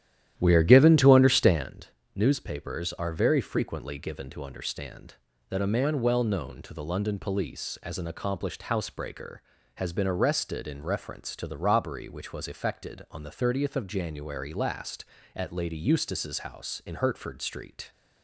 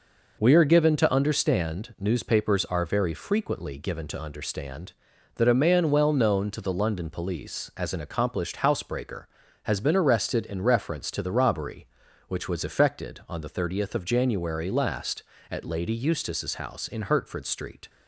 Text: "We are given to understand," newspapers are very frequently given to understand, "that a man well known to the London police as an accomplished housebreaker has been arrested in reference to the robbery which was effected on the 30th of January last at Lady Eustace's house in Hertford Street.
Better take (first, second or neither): second